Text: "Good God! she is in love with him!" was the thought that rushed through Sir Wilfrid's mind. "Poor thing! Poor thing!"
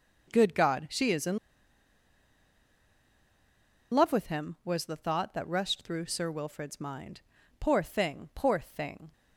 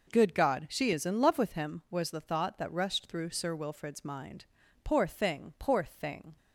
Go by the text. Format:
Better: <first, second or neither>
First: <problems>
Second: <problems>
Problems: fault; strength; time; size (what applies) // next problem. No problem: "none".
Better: second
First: pauses between "in" and "love"; strong; at 1.3 s; 2.5 s long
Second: none